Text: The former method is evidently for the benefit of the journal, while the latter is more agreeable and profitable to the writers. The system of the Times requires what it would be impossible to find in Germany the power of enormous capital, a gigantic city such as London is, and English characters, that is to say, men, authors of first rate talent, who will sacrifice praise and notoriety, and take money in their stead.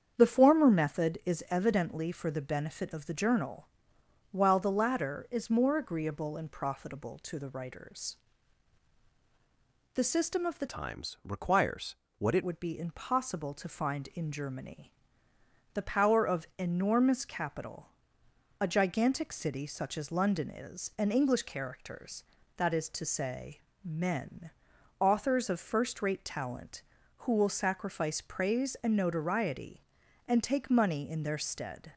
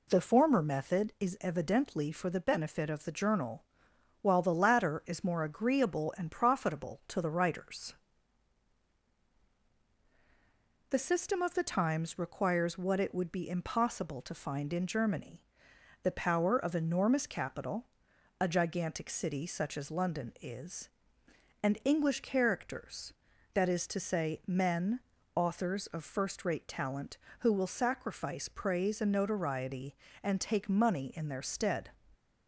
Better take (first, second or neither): second